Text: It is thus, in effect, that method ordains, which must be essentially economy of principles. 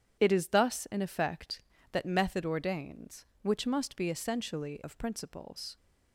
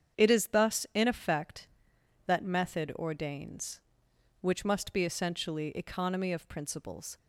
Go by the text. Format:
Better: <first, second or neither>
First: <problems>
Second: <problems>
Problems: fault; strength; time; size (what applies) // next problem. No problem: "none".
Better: second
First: starts louder than the rest; strong; until 1.2 s; 8.5 dB // skips "economy"; at 4.8 s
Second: starts louder than the rest; strong; until 1.2 s; 8 dB